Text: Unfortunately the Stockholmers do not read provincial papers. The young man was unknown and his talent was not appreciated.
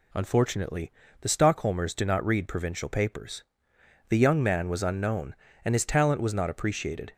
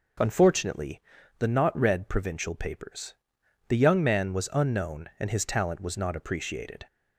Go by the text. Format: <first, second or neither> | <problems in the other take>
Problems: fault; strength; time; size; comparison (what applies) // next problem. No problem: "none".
first | pauses between "Unfortunately" and "the"; at 1.0 s; 0.38 s long; slight in the first // skips "Stockholmers do"; at 1.4 s